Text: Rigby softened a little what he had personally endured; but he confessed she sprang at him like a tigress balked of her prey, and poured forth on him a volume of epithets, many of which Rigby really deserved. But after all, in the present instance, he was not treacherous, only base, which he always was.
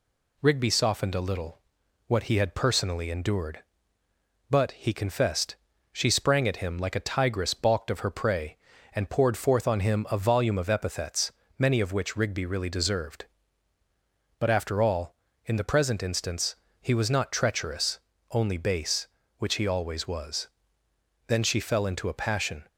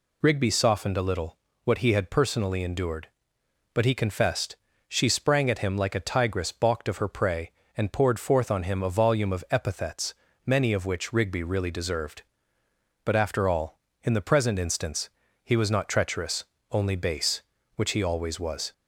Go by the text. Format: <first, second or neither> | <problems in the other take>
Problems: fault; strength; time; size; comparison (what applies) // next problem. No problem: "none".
second | pauses between "little" and "what"; noticeable; at 1.5 s; 0.48 s long; slight in the second // pauses between "confessed" and "she"; slight; at 5.5 s; 0.36 s long; slight in the second // goes on to say "Then she fell into a passion"; from 21.2 s on; 1.4 s long